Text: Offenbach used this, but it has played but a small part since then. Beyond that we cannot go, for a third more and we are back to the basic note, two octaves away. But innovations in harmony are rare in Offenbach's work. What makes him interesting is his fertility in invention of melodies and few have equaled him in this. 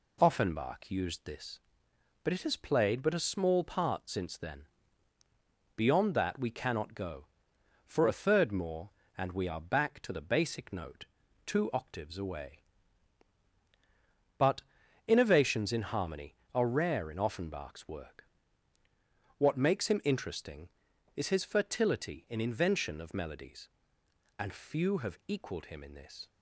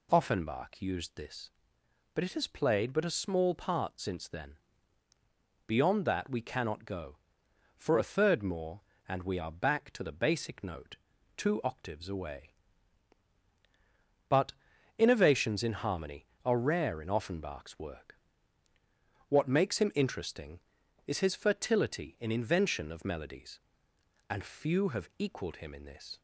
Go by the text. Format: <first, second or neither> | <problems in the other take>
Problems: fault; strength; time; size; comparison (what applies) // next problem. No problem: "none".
second | gets quieter; throughout; 3.5 dB // pauses between "But" and "innovations"; noticeable; at 14.6 s; 0.46 s long; noticeable in the second